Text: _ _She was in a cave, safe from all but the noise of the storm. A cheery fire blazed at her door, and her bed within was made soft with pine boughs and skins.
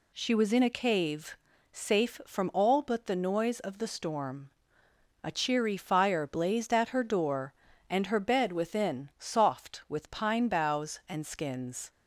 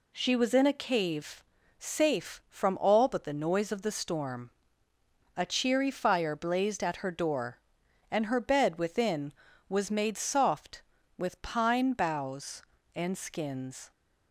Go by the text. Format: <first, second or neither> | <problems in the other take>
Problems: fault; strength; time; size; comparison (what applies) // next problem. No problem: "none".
second | skips "was made"; at 9.1 s